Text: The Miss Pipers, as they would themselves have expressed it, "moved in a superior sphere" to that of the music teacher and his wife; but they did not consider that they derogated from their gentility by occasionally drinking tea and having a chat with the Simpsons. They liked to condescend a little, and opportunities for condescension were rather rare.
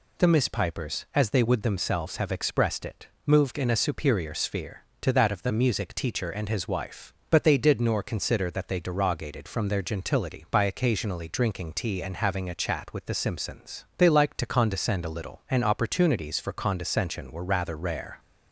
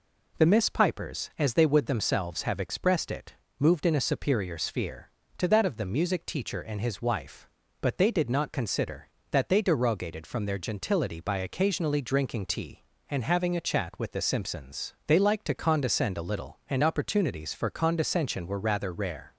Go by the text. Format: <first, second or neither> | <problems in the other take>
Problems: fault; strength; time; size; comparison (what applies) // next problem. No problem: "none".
second | says "nor" for "not"; at 7.8 s